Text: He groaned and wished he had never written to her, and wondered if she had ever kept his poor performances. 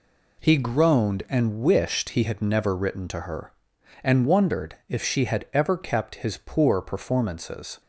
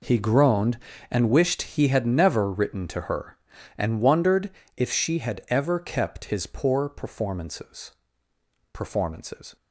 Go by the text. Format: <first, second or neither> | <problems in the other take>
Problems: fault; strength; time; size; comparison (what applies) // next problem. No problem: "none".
first | pauses between "wondered" and "if"; slight; at 4.5 s; 0.25 s long // says "performances" twice; at 8.7 s